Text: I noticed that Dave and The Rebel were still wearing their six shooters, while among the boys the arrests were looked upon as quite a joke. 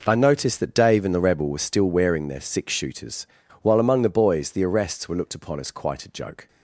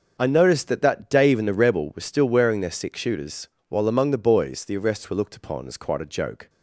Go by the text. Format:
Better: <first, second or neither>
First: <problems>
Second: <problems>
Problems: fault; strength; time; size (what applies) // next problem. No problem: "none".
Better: first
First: none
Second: starts louder than the rest; noticeable; until 1.2 s; 6 dB // says "that" twice; at 0.8 s